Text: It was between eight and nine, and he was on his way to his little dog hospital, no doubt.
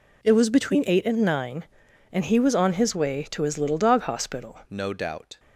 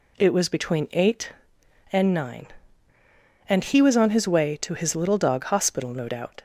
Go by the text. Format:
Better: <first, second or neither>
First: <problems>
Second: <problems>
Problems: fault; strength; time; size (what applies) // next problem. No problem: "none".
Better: second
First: changes voice at "no"; from 4.6 s on; 0.7 s long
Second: none